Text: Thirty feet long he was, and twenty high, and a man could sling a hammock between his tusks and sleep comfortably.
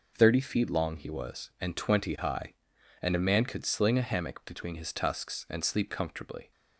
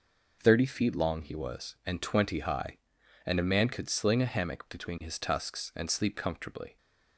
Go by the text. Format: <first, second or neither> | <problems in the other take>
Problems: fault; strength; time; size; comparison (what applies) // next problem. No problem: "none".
neither | none